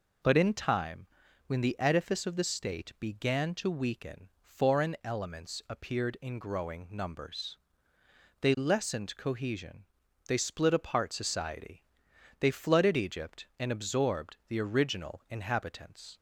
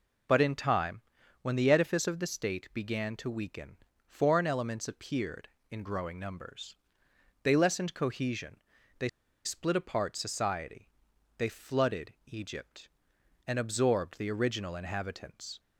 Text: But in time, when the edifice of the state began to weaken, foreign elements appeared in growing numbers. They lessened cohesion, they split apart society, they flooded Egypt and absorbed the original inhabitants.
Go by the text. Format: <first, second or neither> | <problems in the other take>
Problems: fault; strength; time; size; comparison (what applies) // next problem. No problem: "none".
first | pauses between "they" and "split"; slight; at 9.0 s; 0.35 s long